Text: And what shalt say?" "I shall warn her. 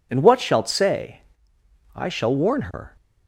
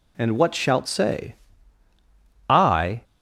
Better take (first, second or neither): first